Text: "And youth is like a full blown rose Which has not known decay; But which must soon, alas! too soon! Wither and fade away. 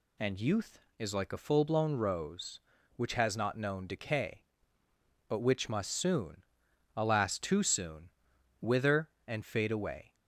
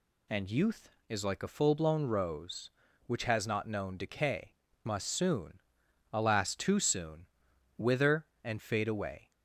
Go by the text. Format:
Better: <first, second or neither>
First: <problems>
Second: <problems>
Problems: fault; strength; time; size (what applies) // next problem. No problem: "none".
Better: first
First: none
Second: skips "But which"; at 4.7 s